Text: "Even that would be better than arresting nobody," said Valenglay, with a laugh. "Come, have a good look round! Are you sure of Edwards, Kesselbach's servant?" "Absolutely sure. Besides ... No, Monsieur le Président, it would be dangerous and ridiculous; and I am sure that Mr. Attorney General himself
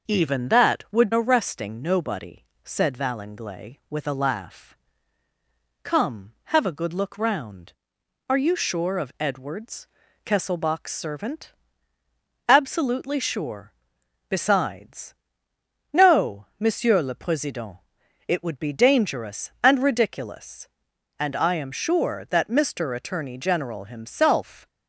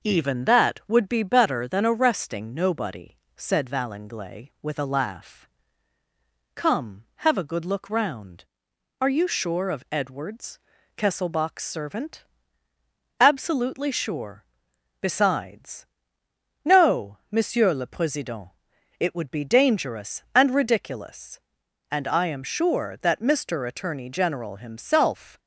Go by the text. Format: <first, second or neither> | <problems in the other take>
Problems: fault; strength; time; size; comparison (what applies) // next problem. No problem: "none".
second | skips "be better than"; at 1.1 s